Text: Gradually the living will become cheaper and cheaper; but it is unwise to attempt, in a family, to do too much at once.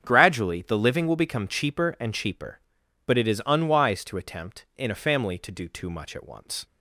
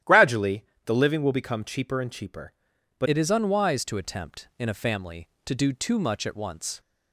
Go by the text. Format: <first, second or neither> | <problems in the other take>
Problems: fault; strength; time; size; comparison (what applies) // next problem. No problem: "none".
first | starts louder than the rest; strong; until 1.2 s; 12 dB; strong in the first // pauses between "Gradually" and "the"; slight; at 0.6 s; 0.22 s long // changes voice at "it"; from 3.0 s on; 3.7 s long